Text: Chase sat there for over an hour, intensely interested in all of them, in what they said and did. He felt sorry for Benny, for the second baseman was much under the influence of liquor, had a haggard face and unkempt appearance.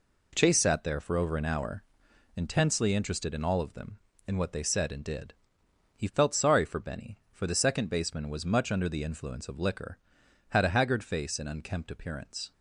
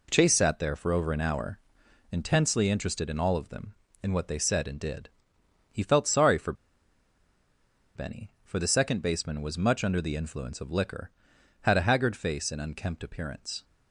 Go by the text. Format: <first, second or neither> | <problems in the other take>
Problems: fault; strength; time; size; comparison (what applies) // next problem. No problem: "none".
first | pauses between "for" and "Benny"; strong; at 6.5 s; 1.4 s long